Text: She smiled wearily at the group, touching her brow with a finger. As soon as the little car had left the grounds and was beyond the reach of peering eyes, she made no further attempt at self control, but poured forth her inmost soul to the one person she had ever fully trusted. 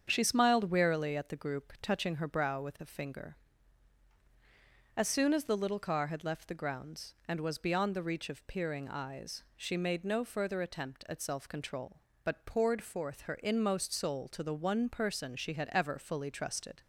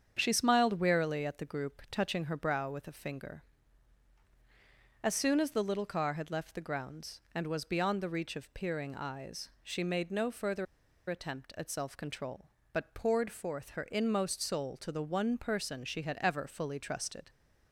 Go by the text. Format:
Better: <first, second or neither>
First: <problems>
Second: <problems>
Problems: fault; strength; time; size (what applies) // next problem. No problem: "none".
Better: first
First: starts louder than the rest; strong; until 1.0 s; 7.5 dB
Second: starts louder than the rest; strong; until 1.1 s; 7.5 dB // pauses between "further" and "attempt"; at 10.6 s; 0.44 s long